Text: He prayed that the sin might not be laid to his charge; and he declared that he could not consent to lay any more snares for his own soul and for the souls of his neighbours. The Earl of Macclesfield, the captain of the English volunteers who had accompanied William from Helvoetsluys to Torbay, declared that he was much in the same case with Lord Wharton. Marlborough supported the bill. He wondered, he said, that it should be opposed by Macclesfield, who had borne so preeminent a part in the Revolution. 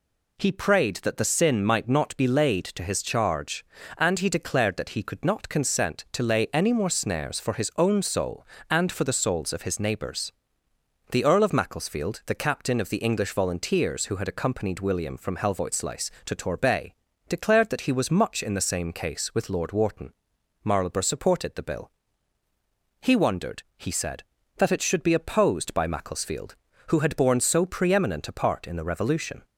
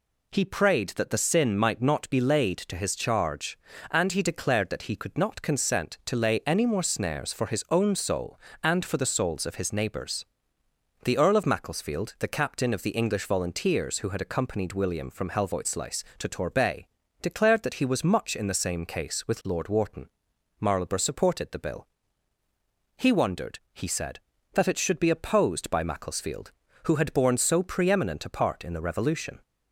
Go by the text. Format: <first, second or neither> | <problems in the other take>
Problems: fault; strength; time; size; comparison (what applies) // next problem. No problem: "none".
neither | none